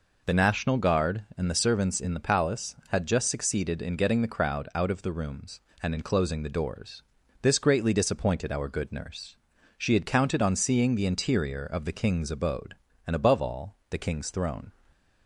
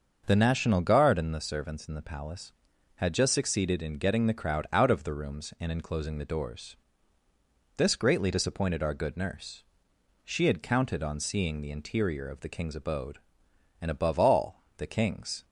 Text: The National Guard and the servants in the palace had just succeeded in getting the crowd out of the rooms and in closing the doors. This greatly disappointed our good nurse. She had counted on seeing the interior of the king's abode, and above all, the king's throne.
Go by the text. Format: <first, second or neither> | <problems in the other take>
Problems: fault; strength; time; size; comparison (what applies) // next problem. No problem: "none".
first | starts louder than the rest; until 1.2 s; 6.5 dB // stops before "throne"; at 15.4 s